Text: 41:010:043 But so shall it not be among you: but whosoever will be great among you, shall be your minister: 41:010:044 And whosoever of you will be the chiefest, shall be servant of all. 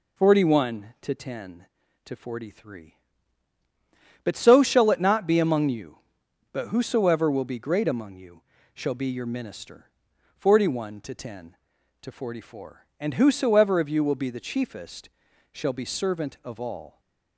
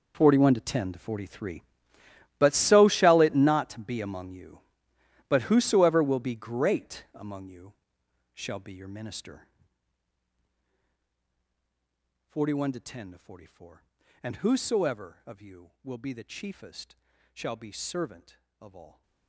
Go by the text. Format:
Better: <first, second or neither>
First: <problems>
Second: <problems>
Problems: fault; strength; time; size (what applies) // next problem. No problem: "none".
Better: first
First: none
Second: gets quieter; strong; throughout; 17 dB